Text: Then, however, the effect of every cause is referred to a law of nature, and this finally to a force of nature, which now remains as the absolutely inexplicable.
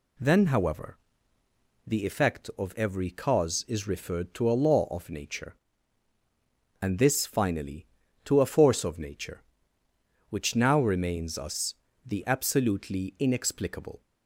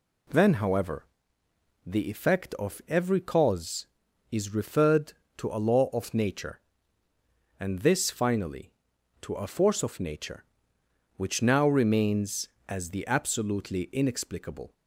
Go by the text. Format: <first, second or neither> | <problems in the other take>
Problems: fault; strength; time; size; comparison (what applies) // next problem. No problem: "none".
second | says "us" for "as"; at 11.3 s